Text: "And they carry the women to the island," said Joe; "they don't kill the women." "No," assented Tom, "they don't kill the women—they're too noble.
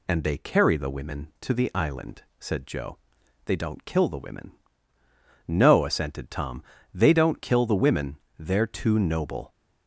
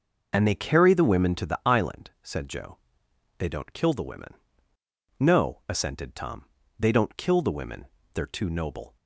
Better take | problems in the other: neither | none

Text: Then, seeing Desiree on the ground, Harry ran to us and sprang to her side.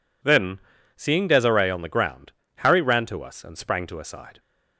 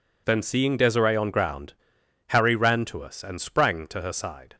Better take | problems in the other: first | skips "the"; at 1.2 s

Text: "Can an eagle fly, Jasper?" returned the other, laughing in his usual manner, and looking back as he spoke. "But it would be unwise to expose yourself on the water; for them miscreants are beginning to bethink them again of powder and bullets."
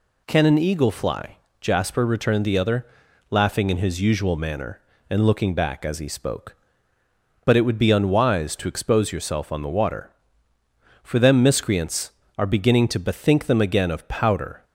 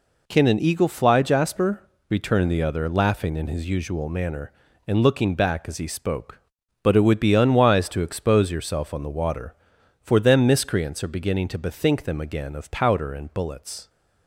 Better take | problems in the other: second | stops before "and bullets"; at 14.6 s

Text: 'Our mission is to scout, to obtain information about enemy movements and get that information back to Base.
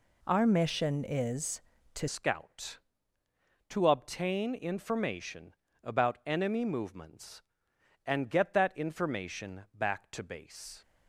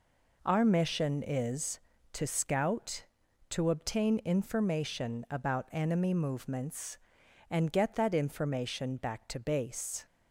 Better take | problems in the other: second | changes voice at "scout"; from 2.0 s on; 8.7 s long // pauses between "information" and "about"; slight; at 5.5 s; 0.28 s long

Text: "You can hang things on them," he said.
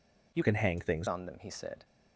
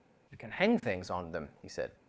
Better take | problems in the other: second | changes voice from "can" to "things"; from 0.4 to 1.0 s; 0.6 s long

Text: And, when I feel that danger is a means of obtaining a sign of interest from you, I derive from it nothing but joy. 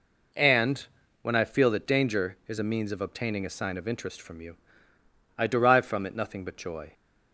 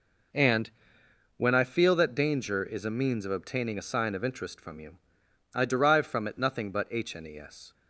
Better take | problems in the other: first | says "hnes" for "joy"; at 6.9 s

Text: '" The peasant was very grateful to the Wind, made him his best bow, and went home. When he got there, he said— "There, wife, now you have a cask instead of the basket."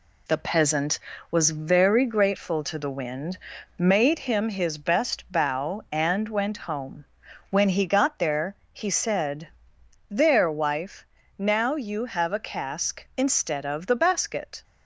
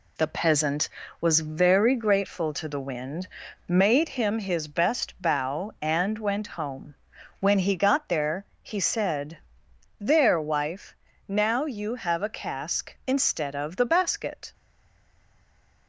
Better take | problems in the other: first | stays silent after the last word; noticeable; from 14.5 s on; 1.3 s long

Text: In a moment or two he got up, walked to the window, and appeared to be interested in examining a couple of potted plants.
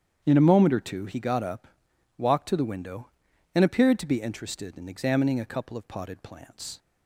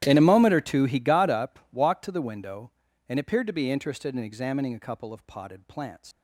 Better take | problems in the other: first | starts louder than the rest; strong; until 1.0 s; 12.5 dB; strong in the first // leaves "plants" unfinished; at 6.1 s; 140 ms

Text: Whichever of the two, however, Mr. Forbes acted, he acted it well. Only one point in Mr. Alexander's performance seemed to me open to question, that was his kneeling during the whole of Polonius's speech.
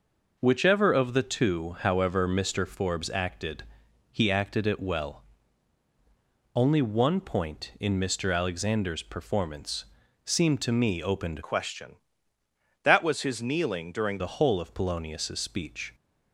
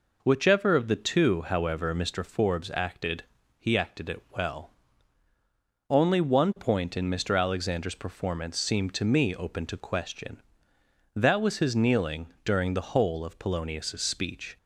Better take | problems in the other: second | pauses between "performance" and "seemed"; at 9.8 s; 0.38 s long // changes voice from "question" to "during"; from 11.4 to 14.1 s; 2.7 s long

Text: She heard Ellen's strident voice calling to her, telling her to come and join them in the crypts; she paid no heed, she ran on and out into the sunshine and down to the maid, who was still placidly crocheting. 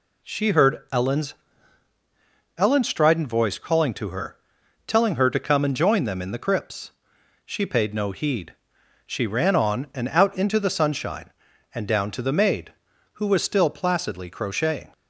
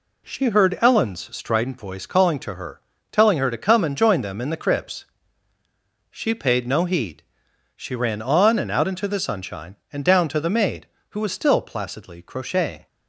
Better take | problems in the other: second | says "Ellen's" twice; at 2.5 s

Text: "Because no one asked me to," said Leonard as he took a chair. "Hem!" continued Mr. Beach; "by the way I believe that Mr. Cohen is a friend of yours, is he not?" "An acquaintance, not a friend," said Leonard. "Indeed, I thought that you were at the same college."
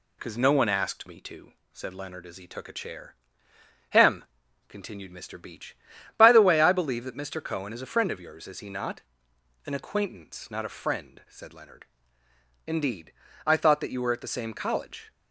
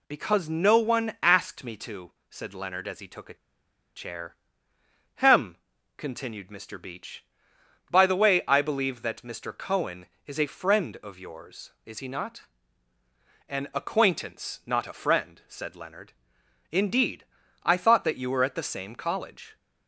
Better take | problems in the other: first | pauses between "a" and "chair"; noticeable; at 3.3 s; 0.61 s long

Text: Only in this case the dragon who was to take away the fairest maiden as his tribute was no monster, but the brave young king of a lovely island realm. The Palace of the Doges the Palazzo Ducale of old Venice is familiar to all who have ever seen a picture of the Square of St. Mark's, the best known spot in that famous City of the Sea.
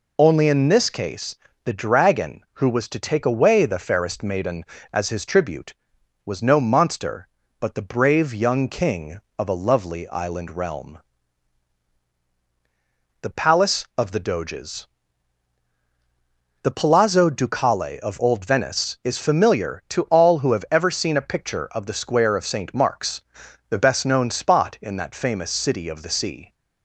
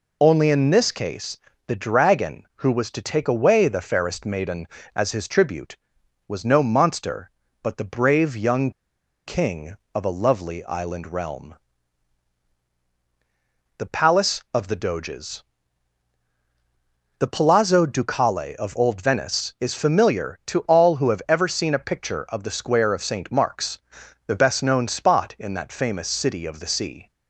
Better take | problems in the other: first | pauses between "case" and "the"; slight; at 1.3 s; 0.28 s long; slight in the first // pauses between "young" and "king"; noticeable; at 8.7 s; 0.55 s long // pauses between "Doges" and "the"; strong; at 15.4 s; 1.7 s long; strong in the first

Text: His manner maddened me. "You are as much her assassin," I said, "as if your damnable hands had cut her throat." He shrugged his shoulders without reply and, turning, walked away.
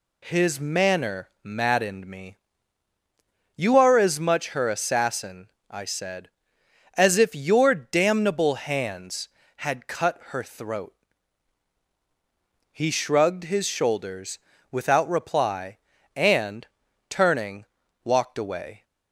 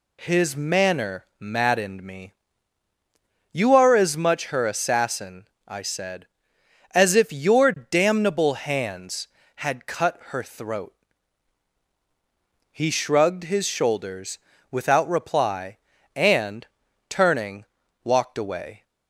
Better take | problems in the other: neither | pauses between "manner" and "maddened"; slight; the same in both // pauses between "shoulders" and "without"; slight; the same in both

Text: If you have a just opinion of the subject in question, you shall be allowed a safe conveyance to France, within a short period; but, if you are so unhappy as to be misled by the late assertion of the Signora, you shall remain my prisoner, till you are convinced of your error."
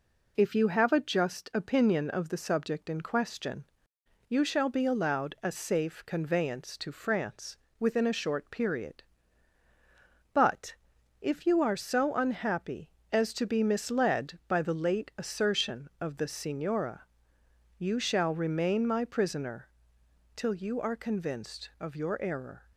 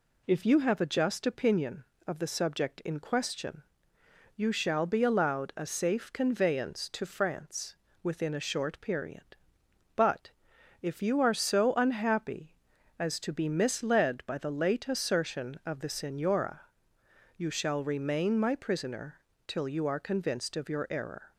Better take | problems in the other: neither | none

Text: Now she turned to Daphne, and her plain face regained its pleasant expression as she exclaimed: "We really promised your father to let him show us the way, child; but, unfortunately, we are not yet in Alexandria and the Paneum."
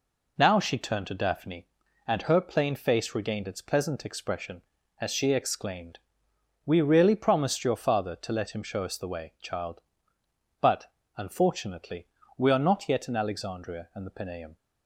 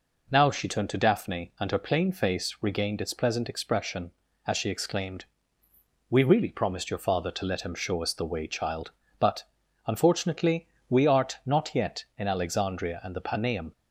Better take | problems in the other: first | says "art" for "are"; at 11.0 s

